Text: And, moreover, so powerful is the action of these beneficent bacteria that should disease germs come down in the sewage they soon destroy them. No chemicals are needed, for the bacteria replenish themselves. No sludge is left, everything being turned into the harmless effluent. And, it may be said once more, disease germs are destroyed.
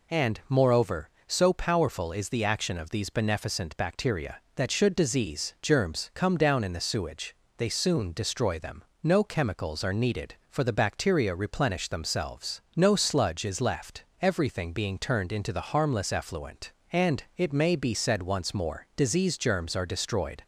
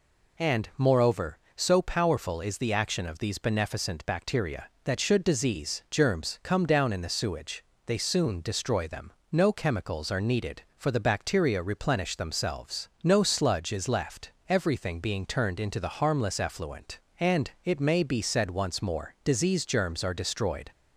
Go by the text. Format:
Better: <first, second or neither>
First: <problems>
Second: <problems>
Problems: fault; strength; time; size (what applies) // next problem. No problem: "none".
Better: neither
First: pauses between "sewage" and "they"; slight; at 7.3 s; 0.22 s long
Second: pauses between "sewage" and "they"; slight; at 7.6 s; 0.22 s long